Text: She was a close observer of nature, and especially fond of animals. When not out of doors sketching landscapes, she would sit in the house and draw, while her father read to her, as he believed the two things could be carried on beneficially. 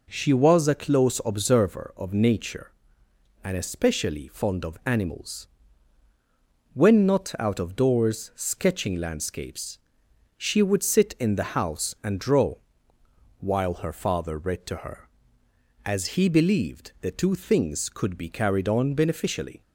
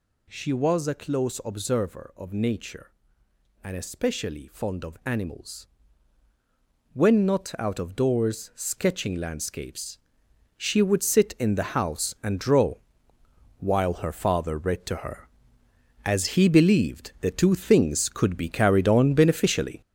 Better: first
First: none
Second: gets louder; strong; throughout; 7.5 dB

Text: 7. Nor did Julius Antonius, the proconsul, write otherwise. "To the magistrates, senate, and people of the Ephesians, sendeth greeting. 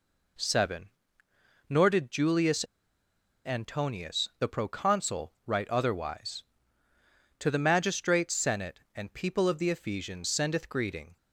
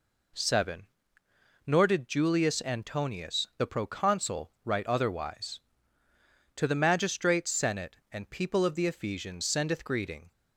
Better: second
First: pauses between "Julius" and "Antonius"; noticeable; at 2.6 s; 0.81 s long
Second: none

